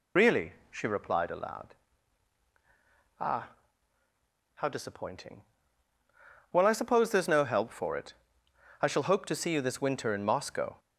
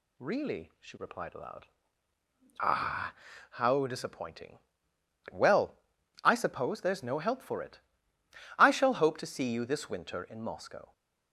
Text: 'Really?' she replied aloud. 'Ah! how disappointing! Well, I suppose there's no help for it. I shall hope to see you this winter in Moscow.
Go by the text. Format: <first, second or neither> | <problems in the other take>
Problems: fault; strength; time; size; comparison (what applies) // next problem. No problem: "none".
second | loses the start of "Really"; at 0.1 s; 65 ms